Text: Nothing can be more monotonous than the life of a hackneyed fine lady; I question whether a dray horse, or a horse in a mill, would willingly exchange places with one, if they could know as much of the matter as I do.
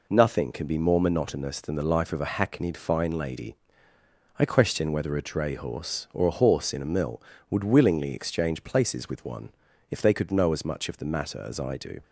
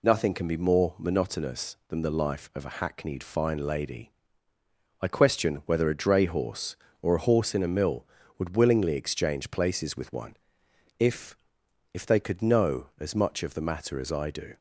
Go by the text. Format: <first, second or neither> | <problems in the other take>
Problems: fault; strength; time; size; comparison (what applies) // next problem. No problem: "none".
first | says "if" twice; at 11.9 s